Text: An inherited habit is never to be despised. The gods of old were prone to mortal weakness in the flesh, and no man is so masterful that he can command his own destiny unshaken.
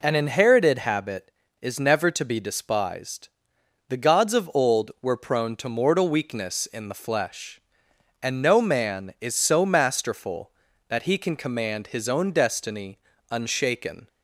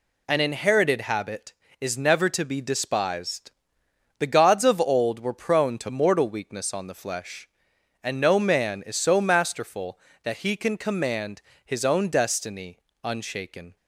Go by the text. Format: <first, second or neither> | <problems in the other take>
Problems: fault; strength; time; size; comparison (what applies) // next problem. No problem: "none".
first | says "on" for "in"; at 6.7 s // pauses between "command" and "his"; slight; at 11.4 s; 0.22 s long // pauses between "destiny" and "unshaken"; slight; at 12.7 s; 0.26 s long; slight in the first